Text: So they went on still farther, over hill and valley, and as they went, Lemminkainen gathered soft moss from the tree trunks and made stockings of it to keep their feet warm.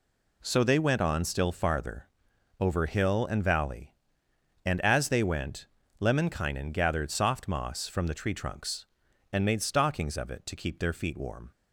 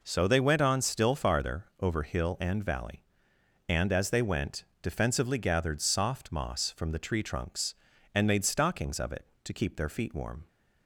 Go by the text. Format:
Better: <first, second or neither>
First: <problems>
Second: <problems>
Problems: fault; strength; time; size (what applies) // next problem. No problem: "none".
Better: first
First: none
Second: says "Defensively" for "Lemminkainen"; at 4.8 s